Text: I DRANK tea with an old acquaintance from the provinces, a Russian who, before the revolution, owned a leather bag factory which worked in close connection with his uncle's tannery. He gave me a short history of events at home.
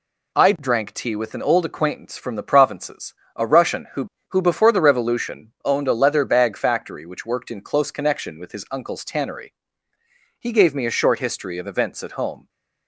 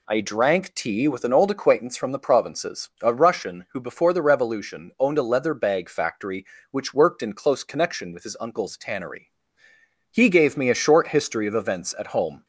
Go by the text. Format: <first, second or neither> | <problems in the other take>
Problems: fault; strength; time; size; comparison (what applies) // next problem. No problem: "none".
second | says "who" twice; at 4.2 s